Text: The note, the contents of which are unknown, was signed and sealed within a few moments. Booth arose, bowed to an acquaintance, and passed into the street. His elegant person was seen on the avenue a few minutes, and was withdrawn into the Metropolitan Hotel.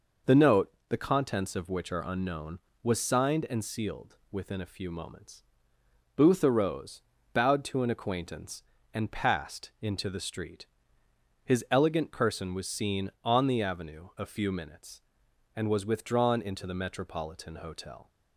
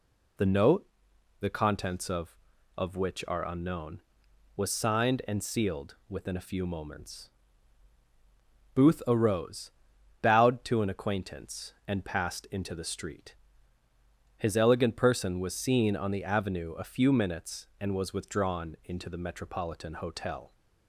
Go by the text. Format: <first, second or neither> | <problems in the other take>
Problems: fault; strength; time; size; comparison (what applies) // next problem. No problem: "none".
first | says "of" twice; at 2.7 s